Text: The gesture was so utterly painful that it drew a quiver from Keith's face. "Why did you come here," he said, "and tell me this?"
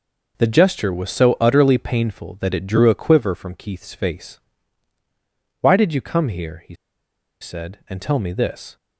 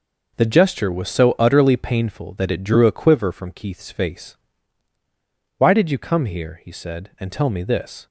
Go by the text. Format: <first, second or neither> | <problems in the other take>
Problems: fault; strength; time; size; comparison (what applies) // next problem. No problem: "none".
second | pauses between "he" and "said"; noticeable; at 6.7 s; 0.66 s long